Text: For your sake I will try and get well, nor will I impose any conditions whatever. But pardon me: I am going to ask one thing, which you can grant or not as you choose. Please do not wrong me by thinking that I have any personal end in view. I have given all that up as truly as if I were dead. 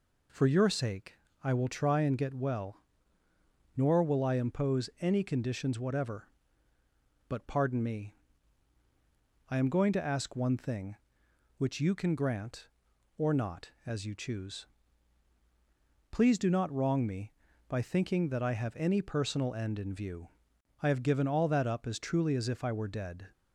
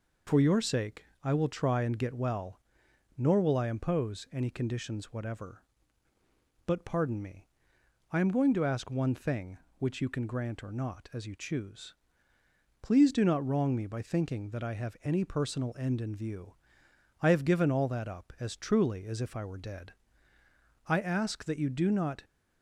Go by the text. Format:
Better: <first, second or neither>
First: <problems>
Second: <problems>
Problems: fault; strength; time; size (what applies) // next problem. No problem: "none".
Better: first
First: pauses between "sake" and "I"; slight; at 1.1 s; 0.26 s long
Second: pauses between "sake" and "I"; slight; at 1.0 s; 0.18 s long // goes on to say "I ask that you do not"; from 20.8 s on; 1.3 s long